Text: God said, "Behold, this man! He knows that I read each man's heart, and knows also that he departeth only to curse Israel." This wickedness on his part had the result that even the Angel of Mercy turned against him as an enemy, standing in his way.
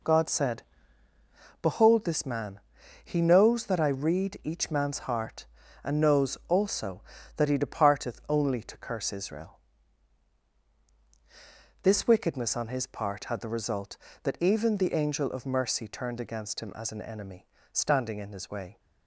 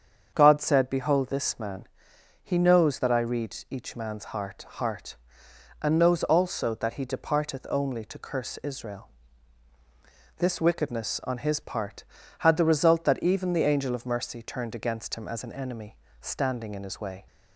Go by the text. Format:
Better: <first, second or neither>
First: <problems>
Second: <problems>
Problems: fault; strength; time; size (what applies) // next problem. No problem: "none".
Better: first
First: none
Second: starts louder than the rest; strong; until 1.3 s; 7 dB // says "heart" twice; at 4.6 s